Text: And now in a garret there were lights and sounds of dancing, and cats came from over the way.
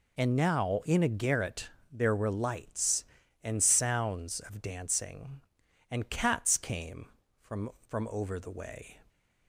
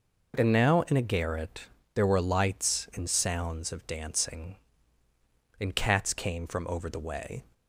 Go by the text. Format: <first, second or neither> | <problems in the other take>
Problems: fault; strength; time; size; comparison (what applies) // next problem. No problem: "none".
second | pauses between "garret" and "there"; slight; at 1.6 s; 0.22 s long; slight in the second // says "from" twice; at 7.8 s